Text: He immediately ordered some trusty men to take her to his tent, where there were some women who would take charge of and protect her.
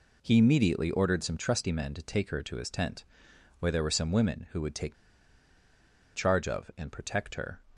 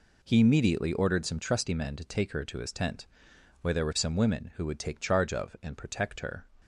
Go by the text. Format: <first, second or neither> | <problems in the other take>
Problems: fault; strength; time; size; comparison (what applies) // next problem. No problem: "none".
second | pauses between "take" and "charge"; at 4.9 s; 1.2 s long